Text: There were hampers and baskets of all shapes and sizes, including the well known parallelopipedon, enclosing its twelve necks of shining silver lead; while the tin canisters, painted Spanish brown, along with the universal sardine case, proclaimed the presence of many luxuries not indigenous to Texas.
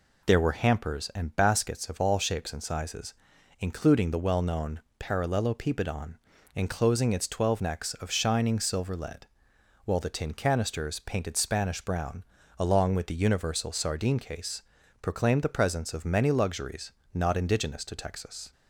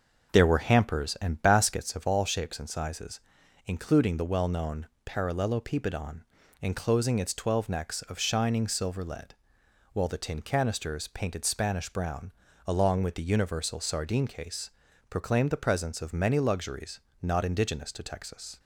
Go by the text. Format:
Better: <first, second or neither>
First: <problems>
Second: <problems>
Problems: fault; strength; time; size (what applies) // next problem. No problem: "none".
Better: first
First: pauses between "known" and "parallelopipedon"; slight; at 4.7 s; 0.20 s long // pauses between "luxuries" and "not"; slight; at 16.9 s; 0.24 s long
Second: starts louder than the rest; noticeable; until 2.2 s; 6 dB // pauses between "known" and "parallelopipedon"; slight; at 4.8 s; 0.20 s long // pauses between "luxuries" and "not"; slight; at 16.9 s; 0.24 s long